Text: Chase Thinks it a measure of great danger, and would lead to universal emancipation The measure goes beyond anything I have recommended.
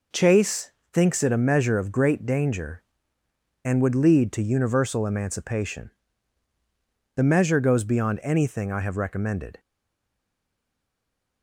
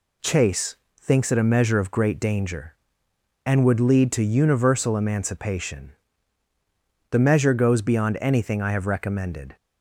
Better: second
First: pauses between "Chase" and "Thinks"; slight; at 0.6 s; 0.26 s long // pauses between "emancipation" and "The"; strong; at 5.8 s; 1.2 s long // stays silent after the last word; noticeable; from 9.5 s on; 1.9 s long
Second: pauses between "Chase" and "Thinks"; slight; at 0.7 s; 0.26 s long // pauses between "emancipation" and "The"; at 5.9 s; 1.1 s long

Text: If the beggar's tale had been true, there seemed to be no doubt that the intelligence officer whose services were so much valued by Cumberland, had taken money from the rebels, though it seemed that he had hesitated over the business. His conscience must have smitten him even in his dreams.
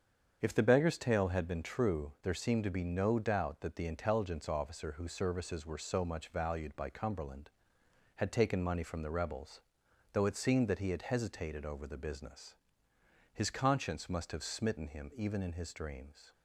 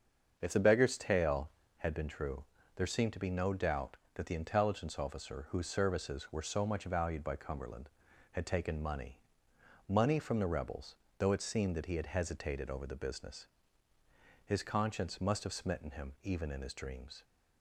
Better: first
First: starts louder than the rest; strong; until 1.4 s; 7.5 dB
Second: starts louder than the rest; until 1.3 s; 7 dB // says "money" twice; at 9.8 s

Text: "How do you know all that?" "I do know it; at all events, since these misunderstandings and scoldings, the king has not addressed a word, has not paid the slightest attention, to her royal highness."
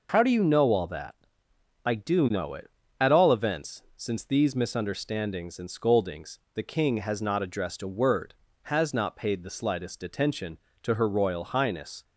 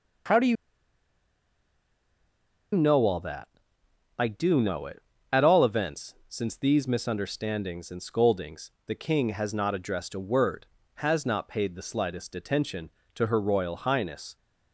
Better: first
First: none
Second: pauses between "you" and "know"; strong; at 0.5 s; 2.2 s long

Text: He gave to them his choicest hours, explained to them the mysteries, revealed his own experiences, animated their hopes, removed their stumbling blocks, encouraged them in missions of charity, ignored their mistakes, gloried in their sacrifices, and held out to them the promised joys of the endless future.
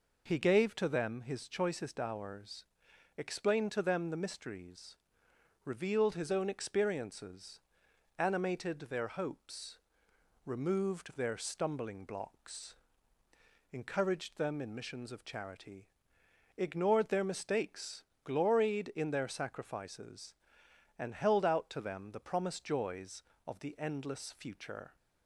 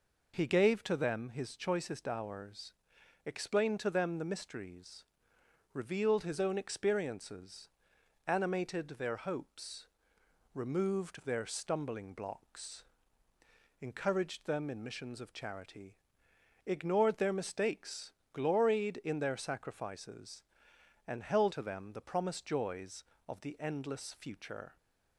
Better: first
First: none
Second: skips "out"; at 21.5 s

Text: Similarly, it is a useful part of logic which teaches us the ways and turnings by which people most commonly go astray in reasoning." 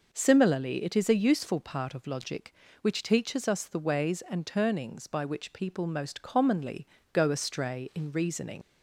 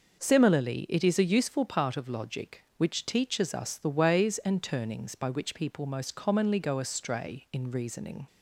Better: second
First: pauses between "commonly" and "go"; slight; at 6.8 s; 0.26 s long // leaves "reasoning" unfinished; at 8.6 s; 95 ms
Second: none

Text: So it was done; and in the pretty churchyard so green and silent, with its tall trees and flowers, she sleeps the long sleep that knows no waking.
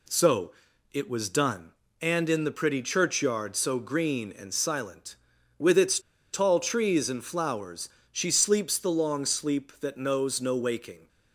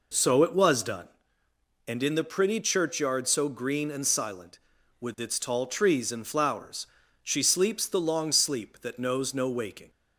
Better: second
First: pauses between "So" and "it"; at 0.5 s; 0.42 s long // pauses between "its" and "tall"; slight; at 5.9 s; 0.33 s long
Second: none

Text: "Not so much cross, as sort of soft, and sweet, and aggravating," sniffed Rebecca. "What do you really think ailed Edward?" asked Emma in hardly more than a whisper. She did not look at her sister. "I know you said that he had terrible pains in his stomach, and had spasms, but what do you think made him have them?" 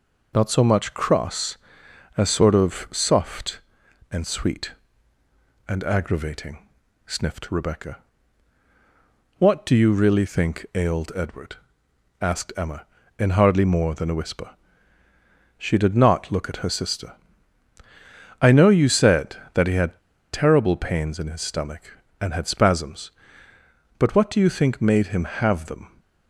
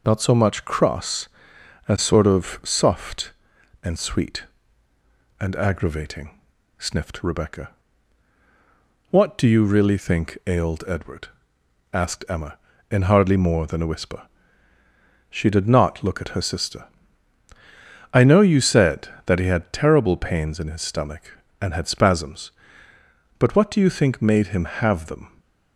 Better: second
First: pauses between "had" and "terrible"; slight; at 19.9 s; 0.32 s long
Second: none

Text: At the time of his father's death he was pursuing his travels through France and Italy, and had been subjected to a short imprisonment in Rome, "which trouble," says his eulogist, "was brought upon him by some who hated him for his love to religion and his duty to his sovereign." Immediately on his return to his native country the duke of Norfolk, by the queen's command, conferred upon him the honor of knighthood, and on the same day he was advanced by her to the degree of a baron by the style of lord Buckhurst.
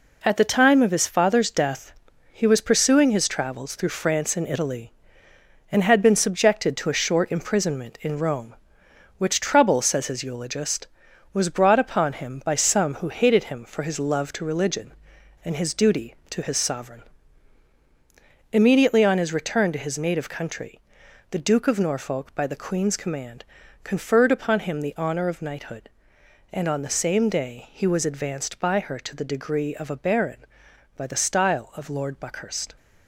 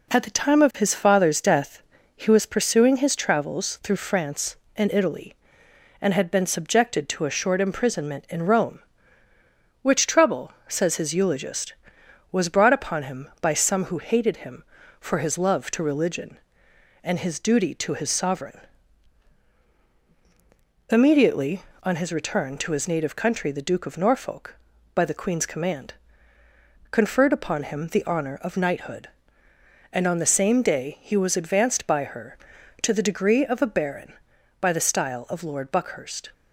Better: second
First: gets quieter; strong; throughout; 7.5 dB // pauses between "death" and "he"; at 1.9 s; 0.38 s long // pauses between "country" and "the"; noticeable; at 20.7 s; 0.52 s long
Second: pauses between "death" and "he"; slight; at 1.8 s; 0.34 s long

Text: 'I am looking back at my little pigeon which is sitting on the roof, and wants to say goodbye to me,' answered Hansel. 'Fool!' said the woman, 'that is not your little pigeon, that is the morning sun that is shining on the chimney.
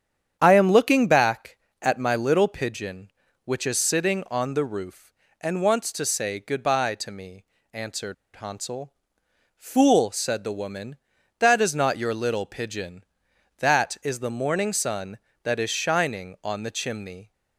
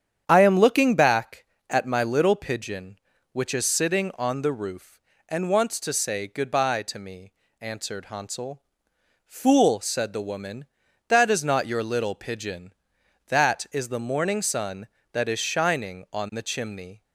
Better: second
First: starts louder than the rest; strong; until 1.4 s; 8.5 dB // pauses between "answered" and "Hansel"; slight; at 8.1 s; 0.21 s long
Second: starts louder than the rest; strong; until 1.2 s; 8.5 dB

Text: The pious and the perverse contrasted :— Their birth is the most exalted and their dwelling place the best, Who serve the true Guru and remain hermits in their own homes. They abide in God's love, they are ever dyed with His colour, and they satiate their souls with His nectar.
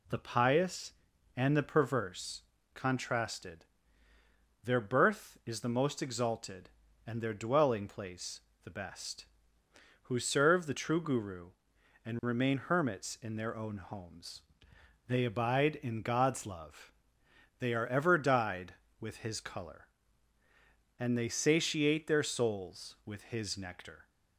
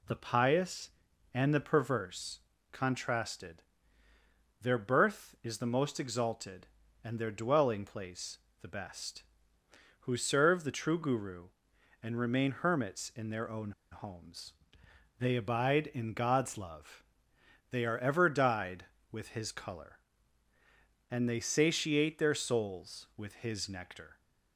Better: first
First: pauses between "perverse" and "contrasted"; slight; at 2.4 s; 0.32 s long // pauses between "place" and "the"; slight; at 8.4 s; 0.22 s long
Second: pauses between "perverse" and "contrasted"; slight; at 2.4 s; 0.32 s long // pauses between "place" and "the"; slight; at 8.3 s; 0.22 s long // pauses between "own" and "homes"; slight; at 13.7 s; 0.20 s long

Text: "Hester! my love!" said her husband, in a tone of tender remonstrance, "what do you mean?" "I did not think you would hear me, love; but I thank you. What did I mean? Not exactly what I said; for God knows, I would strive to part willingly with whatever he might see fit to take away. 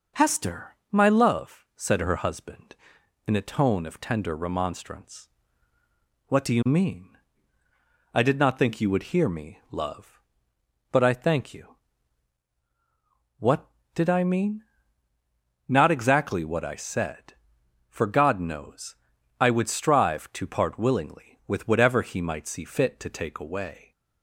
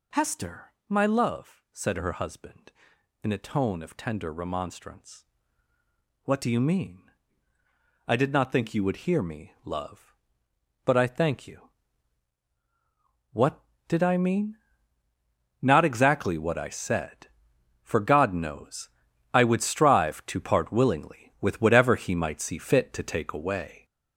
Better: first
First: none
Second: gets louder; throughout; 6 dB

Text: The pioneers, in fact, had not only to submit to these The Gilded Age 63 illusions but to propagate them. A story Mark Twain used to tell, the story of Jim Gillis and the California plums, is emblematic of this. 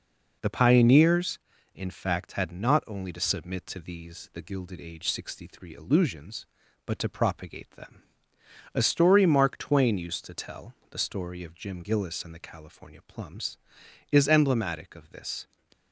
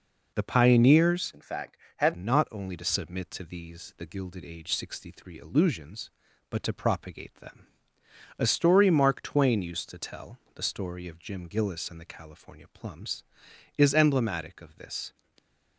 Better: first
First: none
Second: changes voice from "in" to "had"; from 1.3 to 2.1 s; 0.8 s long

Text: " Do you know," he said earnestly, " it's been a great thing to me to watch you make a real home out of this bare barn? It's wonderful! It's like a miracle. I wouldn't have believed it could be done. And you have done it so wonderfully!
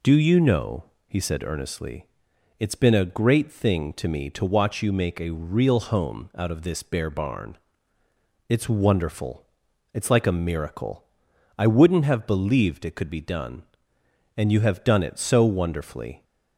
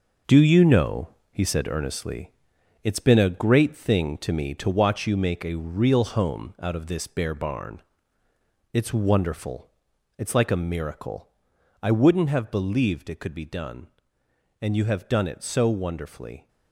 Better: first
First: none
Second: gets quieter; noticeable; throughout; 5 dB

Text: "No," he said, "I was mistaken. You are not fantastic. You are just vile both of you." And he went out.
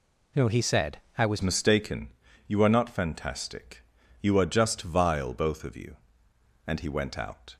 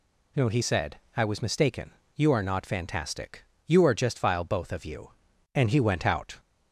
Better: second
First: changes voice at "mistaken"; from 1.4 s on; 6.1 s long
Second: none

